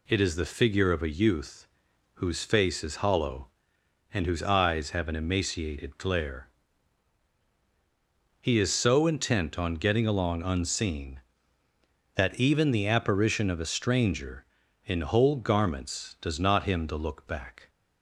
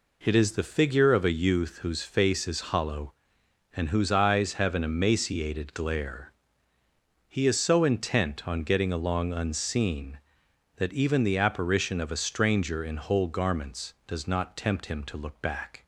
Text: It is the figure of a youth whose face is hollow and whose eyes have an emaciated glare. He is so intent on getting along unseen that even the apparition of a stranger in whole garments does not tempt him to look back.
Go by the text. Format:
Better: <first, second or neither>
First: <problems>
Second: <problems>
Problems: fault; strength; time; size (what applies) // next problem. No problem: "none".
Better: second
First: pauses between "youth" and "whose"; noticeable; at 1.6 s; 0.48 s long // skips "tempt"; at 16.6 s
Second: none